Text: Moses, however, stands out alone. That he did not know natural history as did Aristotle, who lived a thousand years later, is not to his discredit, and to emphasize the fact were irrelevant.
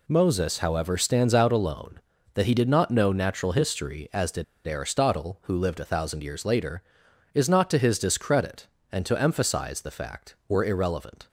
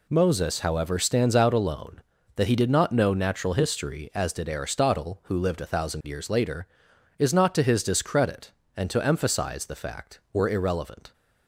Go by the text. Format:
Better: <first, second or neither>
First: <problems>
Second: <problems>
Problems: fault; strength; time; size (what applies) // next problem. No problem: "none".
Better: second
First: pauses between "did" and "Aristotle"; slight; at 4.4 s; 0.21 s long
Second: none